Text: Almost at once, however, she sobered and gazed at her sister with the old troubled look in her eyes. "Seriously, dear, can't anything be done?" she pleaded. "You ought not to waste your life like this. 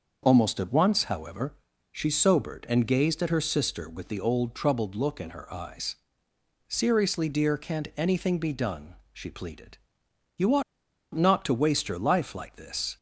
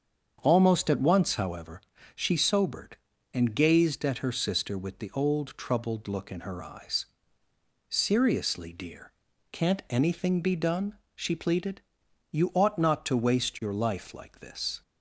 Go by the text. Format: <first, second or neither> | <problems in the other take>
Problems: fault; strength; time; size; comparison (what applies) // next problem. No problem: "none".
second | starts louder than the rest; until 1.2 s; 6.5 dB; strong in the second // pauses between "ought" and "not"; noticeable; at 10.6 s; 0.51 s long